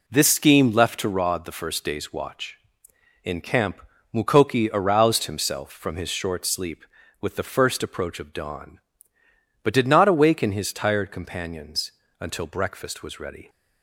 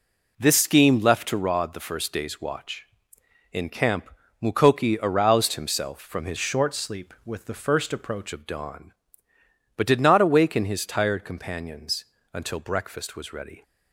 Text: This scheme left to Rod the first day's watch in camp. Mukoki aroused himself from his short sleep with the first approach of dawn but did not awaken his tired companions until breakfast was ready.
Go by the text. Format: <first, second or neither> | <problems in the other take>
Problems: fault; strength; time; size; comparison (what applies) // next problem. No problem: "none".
first | changes voice from "short" to "approach"; from 6.3 to 8.3 s; 2.0 s long // pauses between "companions" and "until"; slight; at 12.0 s; 0.30 s long; slight in the first